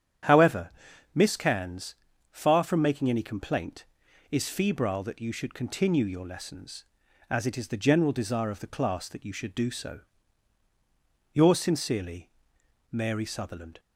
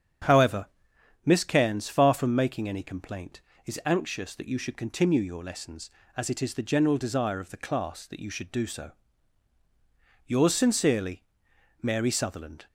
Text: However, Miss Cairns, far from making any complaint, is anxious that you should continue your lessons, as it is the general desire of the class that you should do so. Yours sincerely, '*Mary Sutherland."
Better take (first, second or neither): second